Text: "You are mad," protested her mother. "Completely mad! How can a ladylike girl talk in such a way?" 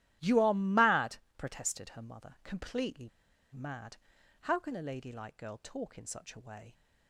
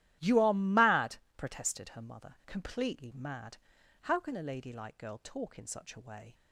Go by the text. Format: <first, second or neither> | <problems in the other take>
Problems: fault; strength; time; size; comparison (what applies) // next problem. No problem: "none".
second | starts louder than the rest; strong; until 1.4 s; 13 dB; strong in the second // pauses between "Completely" and "mad"; at 3.0 s; 0.44 s long